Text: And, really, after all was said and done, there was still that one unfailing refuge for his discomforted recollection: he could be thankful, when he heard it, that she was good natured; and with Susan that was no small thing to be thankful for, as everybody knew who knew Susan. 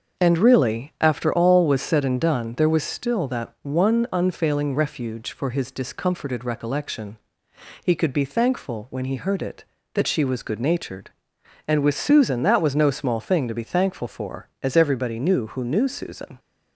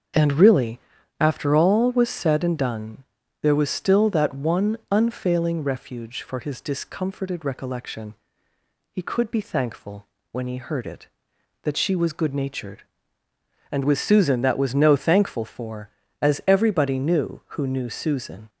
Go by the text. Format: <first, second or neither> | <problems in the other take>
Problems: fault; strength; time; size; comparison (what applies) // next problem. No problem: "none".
first | starts louder than the rest; until 1.5 s; 7 dB; also in the first // skips "small thing to be"; at 14.9 s